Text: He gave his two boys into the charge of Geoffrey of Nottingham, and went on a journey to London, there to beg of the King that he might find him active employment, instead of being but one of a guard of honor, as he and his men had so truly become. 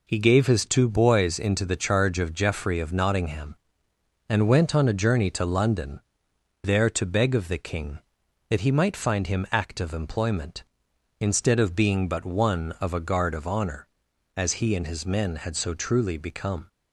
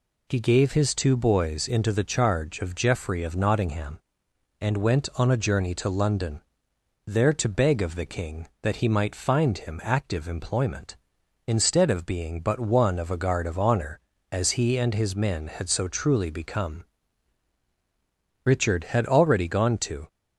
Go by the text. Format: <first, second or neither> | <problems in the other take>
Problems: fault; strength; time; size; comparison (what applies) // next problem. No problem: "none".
first | goes on to say "Richard had already gone to"; from 18.4 s on; 1.6 s long